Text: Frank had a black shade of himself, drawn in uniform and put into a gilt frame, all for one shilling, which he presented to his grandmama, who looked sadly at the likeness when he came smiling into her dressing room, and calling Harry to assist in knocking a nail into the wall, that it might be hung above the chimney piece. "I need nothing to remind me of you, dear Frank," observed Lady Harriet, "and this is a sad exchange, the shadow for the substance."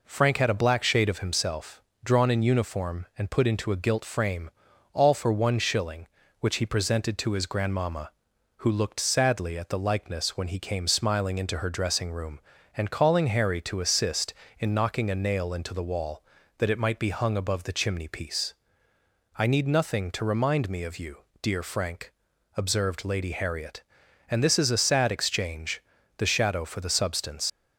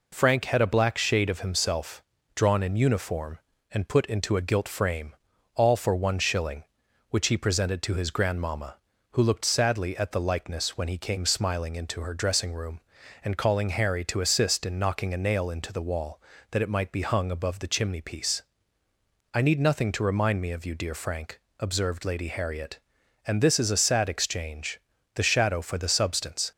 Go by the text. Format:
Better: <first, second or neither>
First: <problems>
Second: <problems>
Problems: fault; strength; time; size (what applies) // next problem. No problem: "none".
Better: second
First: leaves "substance" unfinished; at 27.4 s; 95 ms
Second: none